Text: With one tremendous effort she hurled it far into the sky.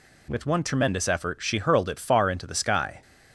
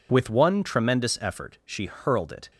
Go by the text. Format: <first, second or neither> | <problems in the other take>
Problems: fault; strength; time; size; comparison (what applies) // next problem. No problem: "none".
first | stops before "far into the sky"; at 2.5 s